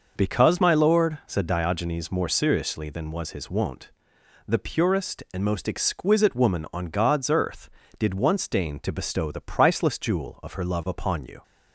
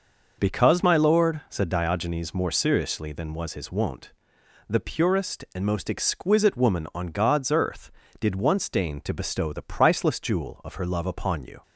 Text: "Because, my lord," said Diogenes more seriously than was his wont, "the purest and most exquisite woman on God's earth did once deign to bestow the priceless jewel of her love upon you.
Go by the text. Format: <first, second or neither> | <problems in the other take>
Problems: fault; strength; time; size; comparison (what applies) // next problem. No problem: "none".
neither | none